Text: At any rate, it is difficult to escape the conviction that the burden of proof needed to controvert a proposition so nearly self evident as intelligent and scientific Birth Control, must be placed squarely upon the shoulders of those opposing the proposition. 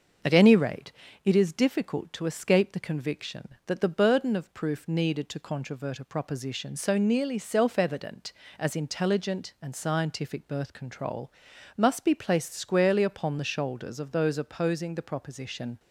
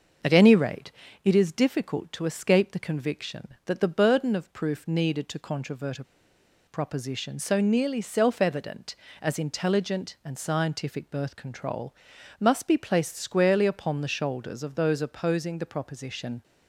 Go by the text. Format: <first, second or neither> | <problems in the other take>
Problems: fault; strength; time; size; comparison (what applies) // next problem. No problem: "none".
first | starts louder than the rest; until 1.5 s; 6 dB; also in the first // pauses between "a" and "proposition"; noticeable; at 6.0 s; 0.63 s long